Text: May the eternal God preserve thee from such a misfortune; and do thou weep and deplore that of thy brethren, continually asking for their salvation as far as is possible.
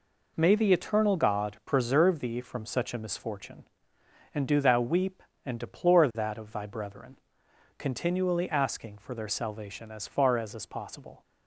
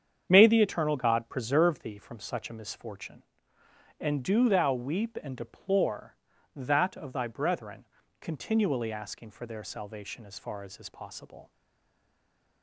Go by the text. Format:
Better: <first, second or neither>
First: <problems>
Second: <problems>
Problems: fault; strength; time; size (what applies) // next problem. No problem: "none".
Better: first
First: none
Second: starts louder than the rest; strong; until 1.3 s; 8 dB // stays silent after the last word; from 11.5 s on; 1.1 s long